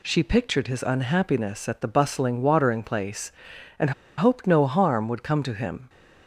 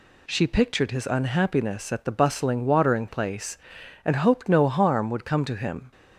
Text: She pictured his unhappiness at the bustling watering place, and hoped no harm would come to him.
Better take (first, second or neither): second